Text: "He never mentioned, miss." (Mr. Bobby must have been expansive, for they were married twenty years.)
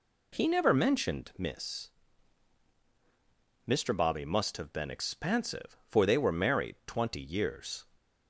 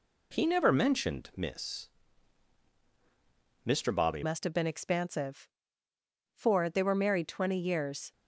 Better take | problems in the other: first | changes voice at "must"; from 4.2 s on; 3.9 s long

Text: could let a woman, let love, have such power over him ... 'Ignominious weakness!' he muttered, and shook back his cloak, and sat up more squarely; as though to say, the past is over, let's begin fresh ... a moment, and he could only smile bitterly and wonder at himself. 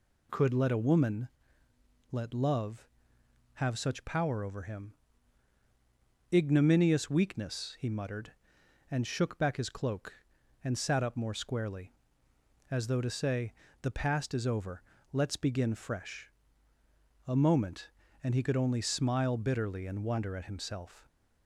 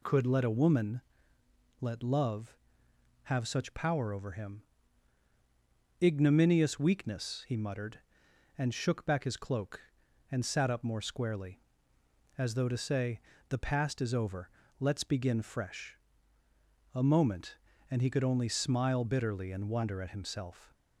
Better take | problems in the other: neither | none

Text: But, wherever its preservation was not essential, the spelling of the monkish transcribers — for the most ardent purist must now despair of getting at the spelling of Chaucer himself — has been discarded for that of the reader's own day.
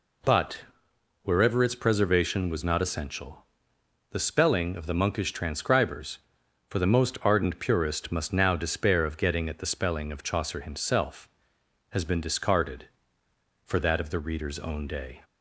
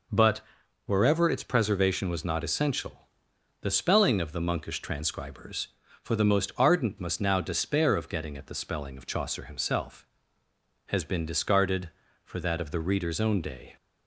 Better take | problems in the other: first | skips "purist"; at 6.9 s

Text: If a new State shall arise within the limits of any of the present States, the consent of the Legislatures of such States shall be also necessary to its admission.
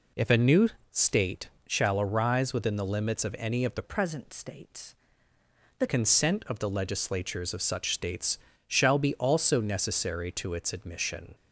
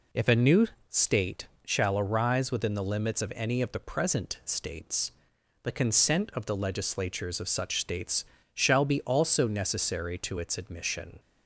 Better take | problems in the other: second | pauses between "new" and "State"; slight; at 0.6 s; 0.22 s long; slight in the second // pauses between "State" and "shall"; slight; at 1.4 s; 0.16 s long; slight in the second // changes voice from "present" to "the"; from 3.8 to 5.8 s; 2.0 s long // pauses between "States" and "shall"; slight; at 8.3 s; 0.28 s long; slight in the second

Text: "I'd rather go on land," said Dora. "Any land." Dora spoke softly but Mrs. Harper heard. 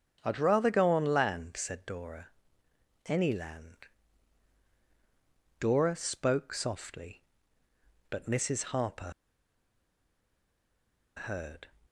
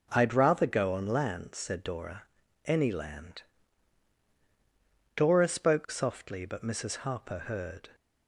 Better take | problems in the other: second | starts louder than the rest; strong; until 1.2 s; 7.5 dB // pauses between "Harper" and "heard"; strong; at 9.1 s; 2.0 s long

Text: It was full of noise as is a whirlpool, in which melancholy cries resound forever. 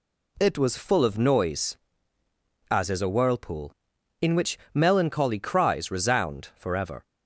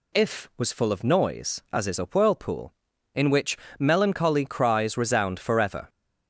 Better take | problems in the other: first | says "If" for "It"; at 0.1 s // pauses between "which" and "melancholy"; slight; at 3.5 s; 0.22 s long; slight in the first

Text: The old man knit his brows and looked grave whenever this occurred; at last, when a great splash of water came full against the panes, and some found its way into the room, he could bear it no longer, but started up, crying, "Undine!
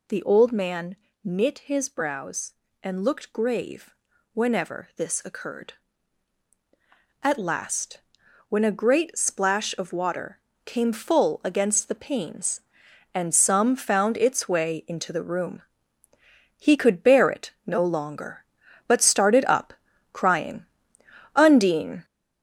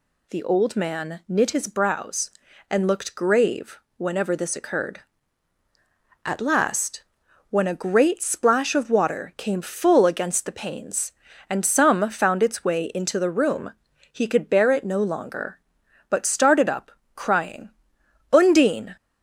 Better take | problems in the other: second | gets louder; noticeable; throughout; 5.5 dB // pauses between "man" and "knit"; slight; at 0.9 s; 0.28 s long // pauses between "grave" and "whenever"; at 3.9 s; 0.40 s long; slight in the second // pauses between "water" and "came"; slight; at 10.4 s; 0.24 s long // pauses between "it" and "no"; slight; at 17.5 s; 0.16 s long

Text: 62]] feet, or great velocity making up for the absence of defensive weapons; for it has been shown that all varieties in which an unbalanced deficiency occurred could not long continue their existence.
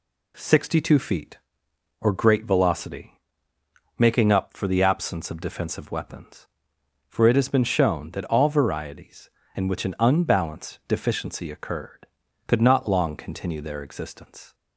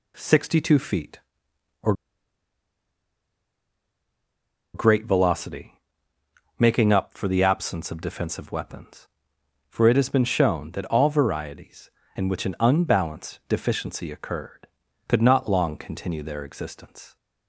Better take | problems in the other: first | pauses between "or" and "great"; strong; at 1.9 s; 2.8 s long // pauses between "velocity" and "making"; noticeable; at 5.8 s; 0.80 s long; noticeable in the first

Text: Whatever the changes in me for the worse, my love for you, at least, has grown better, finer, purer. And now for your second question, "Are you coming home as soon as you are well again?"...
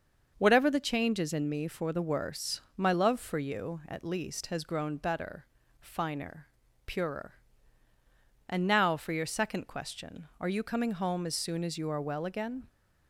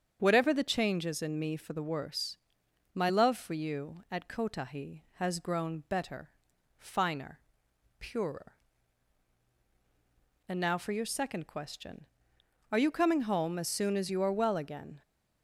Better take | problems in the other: first | starts louder than the rest; strong; until 1.2 s; 8 dB; also in the first // says "kotahi" for "least"; at 4.2 s

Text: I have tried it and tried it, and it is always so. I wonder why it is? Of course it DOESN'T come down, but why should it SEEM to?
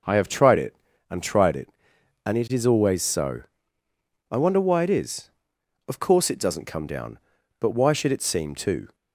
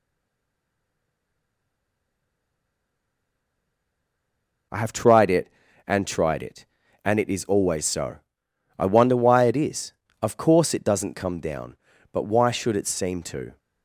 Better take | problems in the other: first | stays silent before the first word; strong; until 4.7 s; 4.7 s long

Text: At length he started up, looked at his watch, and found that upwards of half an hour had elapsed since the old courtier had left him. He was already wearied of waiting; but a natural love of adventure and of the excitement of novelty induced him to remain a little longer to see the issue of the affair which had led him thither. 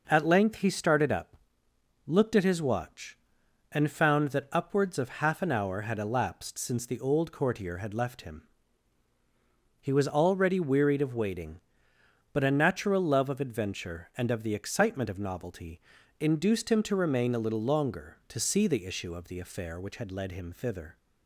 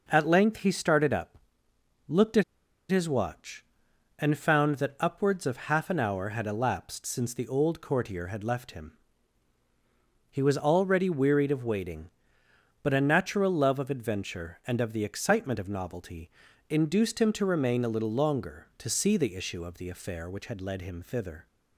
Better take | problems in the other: first | pauses between "at" and "his"; noticeable; at 2.4 s; 0.47 s long // pauses between "novelty" and "induced"; at 16.2 s; 0.40 s long; also in the first

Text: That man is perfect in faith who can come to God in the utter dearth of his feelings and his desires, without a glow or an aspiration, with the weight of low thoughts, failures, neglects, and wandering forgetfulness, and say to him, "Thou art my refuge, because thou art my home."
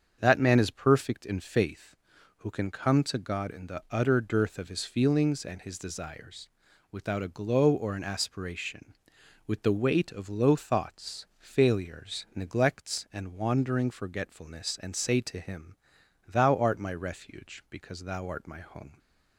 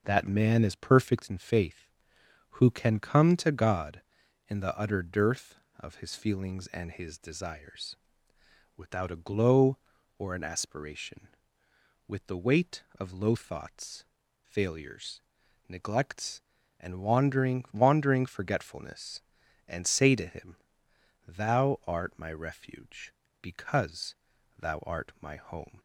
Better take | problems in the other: first | starts louder than the rest; noticeable; until 1.0 s; 6 dB; strong in the first // says "wandering" twice; at 17.7 s // pauses between "because" and "thou"; at 24.1 s; 0.44 s long

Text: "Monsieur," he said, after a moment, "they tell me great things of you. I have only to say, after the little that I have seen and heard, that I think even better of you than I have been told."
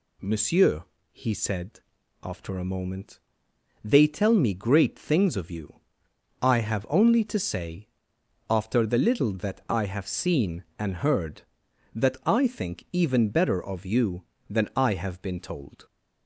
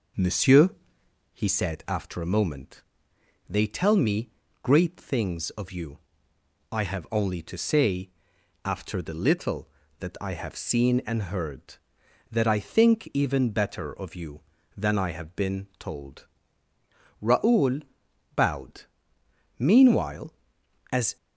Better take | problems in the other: first | pauses between "me" and "great"; slight; at 4.3 s; 0.32 s long // goes on to say "Raoul bowed Meanwhile as"; strong; from 17.2 s on; 3.9 s long

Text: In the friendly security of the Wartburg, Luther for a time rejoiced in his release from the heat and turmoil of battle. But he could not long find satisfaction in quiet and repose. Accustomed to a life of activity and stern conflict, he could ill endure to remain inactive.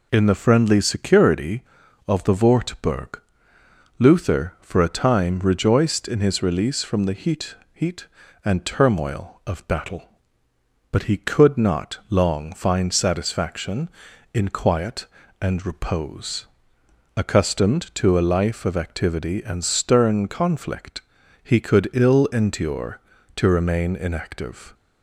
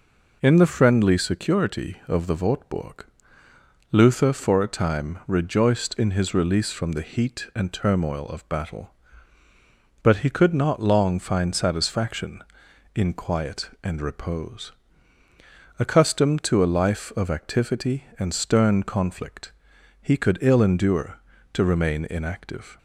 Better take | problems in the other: second | says "heat" twice; at 7.7 s

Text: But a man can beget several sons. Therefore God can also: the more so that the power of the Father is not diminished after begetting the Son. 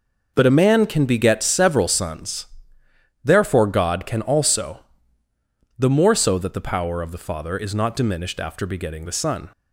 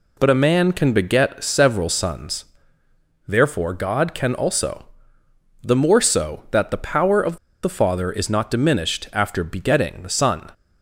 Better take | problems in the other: first | pauses between "of" and "the"; slight; at 7.3 s; 0.27 s long

